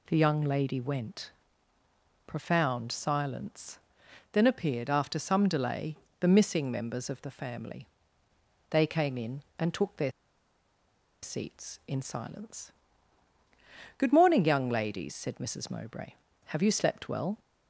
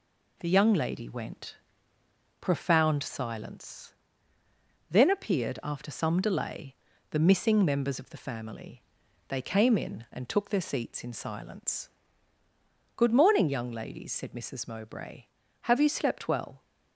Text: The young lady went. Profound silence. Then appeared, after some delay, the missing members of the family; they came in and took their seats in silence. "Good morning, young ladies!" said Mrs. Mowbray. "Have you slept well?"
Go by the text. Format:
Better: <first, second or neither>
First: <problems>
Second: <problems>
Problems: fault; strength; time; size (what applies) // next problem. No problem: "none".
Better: second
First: pauses between "their" and "seats"; at 10.1 s; 1.1 s long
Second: none